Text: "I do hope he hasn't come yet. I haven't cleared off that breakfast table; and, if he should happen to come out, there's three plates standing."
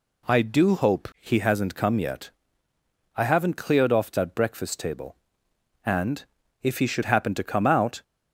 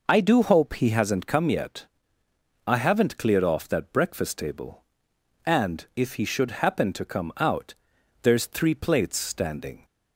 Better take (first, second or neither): second